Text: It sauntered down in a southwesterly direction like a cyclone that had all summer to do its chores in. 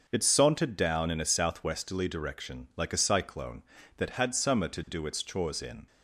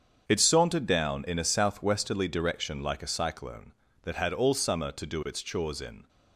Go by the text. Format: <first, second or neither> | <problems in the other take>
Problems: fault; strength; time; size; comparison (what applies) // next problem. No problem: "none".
second | starts louder than the rest; until 1.0 s; 6.5 dB; strong in the second // skips "all"; at 4.3 s